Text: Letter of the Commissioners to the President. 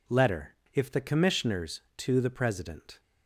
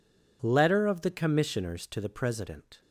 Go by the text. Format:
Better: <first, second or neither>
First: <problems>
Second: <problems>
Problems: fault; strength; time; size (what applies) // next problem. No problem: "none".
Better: second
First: says "if" for "of"; at 0.7 s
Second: none